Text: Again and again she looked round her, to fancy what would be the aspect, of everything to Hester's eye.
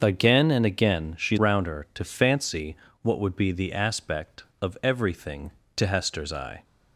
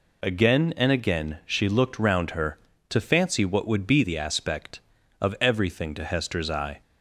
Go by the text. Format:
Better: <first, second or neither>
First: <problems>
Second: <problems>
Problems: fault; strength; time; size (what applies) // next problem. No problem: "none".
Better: second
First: starts louder than the rest; until 1.0 s; 6.5 dB // skips "looked"; at 1.3 s // pauses between "fancy" and "what"; slight; at 2.7 s; 0.24 s long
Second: none